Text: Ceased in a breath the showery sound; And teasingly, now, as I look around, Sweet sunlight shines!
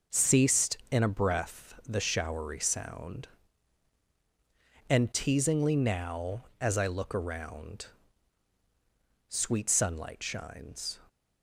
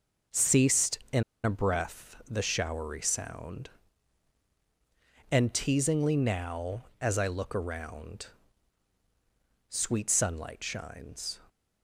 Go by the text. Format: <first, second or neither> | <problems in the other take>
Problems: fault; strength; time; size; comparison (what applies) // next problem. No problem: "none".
first | pauses between "in" and "a"; slight; at 1.2 s; 0.20 s long